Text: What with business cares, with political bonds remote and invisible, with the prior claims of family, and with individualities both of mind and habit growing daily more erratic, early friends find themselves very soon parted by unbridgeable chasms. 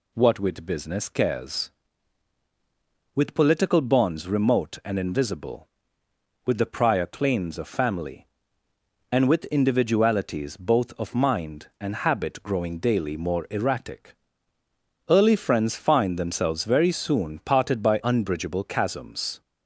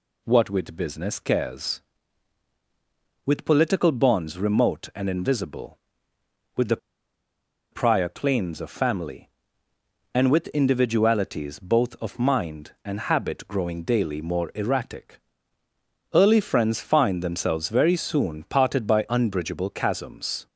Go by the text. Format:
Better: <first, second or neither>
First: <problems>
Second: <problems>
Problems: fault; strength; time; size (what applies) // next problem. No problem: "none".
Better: first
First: none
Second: pauses between "the" and "prior"; noticeable; at 6.7 s; 0.94 s long